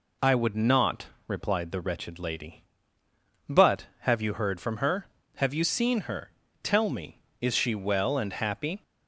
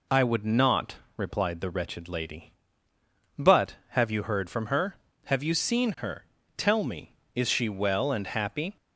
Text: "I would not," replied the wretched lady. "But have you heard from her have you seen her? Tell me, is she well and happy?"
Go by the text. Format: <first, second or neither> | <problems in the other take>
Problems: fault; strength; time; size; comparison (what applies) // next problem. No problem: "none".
neither | none